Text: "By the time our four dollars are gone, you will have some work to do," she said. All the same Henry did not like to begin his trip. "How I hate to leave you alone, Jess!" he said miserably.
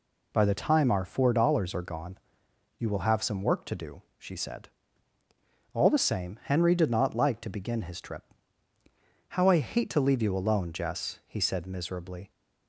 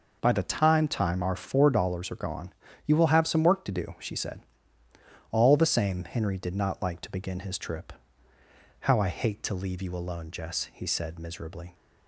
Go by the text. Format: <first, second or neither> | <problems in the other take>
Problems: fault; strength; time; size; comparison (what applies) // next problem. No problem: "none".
first | says "time" twice; at 0.8 s